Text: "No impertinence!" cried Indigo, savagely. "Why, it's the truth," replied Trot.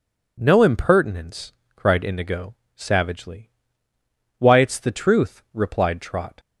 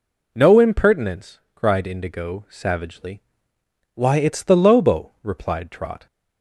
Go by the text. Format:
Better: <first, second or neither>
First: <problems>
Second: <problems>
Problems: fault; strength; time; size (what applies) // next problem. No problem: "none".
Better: first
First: none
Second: says "lobo" for "truth"; at 4.5 s